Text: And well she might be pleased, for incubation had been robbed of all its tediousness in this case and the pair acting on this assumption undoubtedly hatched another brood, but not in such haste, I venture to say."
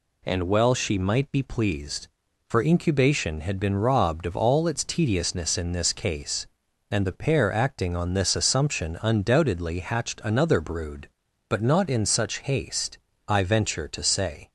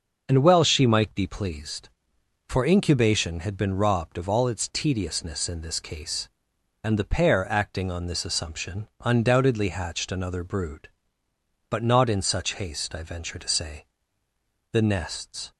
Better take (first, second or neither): first